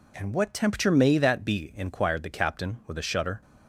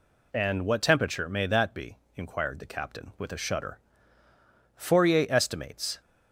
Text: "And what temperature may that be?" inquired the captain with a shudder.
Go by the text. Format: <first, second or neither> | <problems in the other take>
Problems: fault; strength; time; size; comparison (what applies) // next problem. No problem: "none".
first | goes on to say "Fourier estimates"; noticeable; from 4.7 s on; 1.2 s long